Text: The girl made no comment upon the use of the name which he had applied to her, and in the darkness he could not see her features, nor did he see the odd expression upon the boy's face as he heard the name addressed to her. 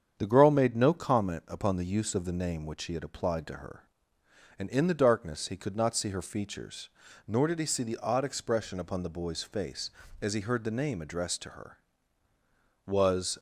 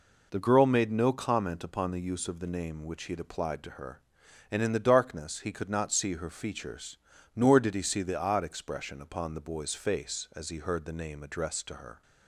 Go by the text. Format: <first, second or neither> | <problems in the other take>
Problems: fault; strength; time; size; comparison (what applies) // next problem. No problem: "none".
second | starts louder than the rest; strong; until 1.1 s; 8 dB // goes on to say "Was"; from 12.8 s on; 0.52 s long